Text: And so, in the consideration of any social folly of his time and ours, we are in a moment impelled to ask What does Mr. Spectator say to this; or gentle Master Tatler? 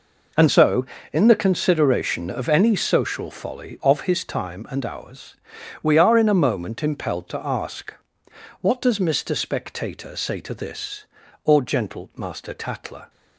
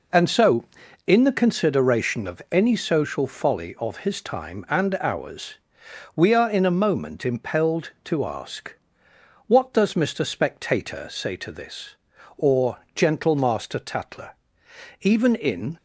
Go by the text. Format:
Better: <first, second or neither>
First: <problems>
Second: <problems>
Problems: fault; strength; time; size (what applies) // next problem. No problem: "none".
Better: first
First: pauses between "ask" and "What"; noticeable; at 7.9 s; 0.70 s long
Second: pauses between "ask" and "What"; noticeable; at 8.7 s; 0.72 s long // pauses between "or" and "gentle"; slight; at 12.7 s; 0.16 s long // goes on to say "Even in"; noticeable; from 15.0 s on; 0.76 s long